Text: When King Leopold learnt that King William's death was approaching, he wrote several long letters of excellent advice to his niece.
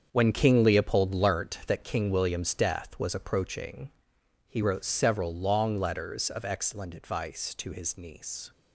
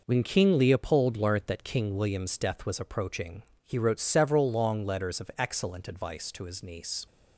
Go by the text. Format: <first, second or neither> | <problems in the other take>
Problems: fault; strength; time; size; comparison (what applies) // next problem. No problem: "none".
second | gets quieter; strong; throughout; 10 dB